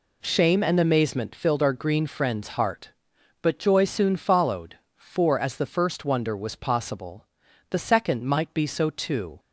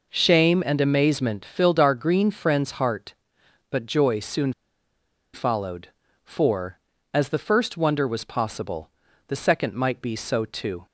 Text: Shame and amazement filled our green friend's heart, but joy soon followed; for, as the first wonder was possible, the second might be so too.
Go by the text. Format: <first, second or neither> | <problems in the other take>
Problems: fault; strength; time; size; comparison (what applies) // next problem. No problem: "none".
first | pauses between "soon" and "followed"; noticeable; at 4.5 s; 0.82 s long